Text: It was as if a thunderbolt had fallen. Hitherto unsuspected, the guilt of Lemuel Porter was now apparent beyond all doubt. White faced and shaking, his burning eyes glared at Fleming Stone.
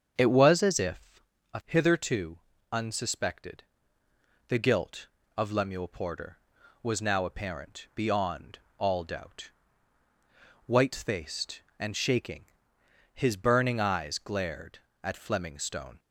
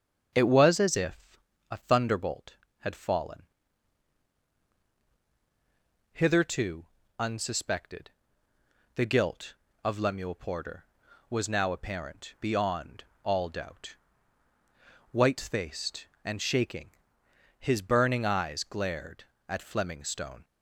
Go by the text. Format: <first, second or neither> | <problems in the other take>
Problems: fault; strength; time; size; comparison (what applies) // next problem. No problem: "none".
second | starts louder than the rest; strong; until 1.1 s; 7 dB; strong in the second // pauses between "if" and "a"; slight; at 1.2 s; 0.32 s long; slight in the second // skips "thunderbolt had fallen"; at 1.6 s // pauses between "Hitherto" and "unsuspected"; slight; at 2.3 s; 0.34 s long; slight in the second // pauses between "beyond" and "all"; slight; at 8.5 s; 0.20 s long; slight in the second